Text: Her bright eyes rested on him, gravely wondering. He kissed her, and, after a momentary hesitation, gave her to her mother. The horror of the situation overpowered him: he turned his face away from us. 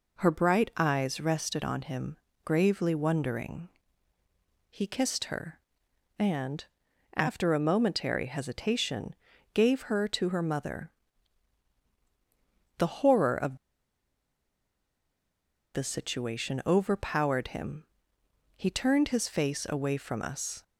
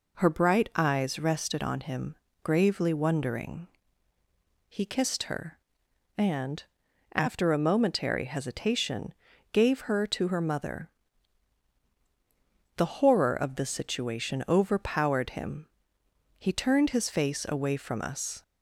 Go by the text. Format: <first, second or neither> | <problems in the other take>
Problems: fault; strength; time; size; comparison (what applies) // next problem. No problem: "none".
second | pauses between "of" and "the"; strong; at 13.5 s; 2.1 s long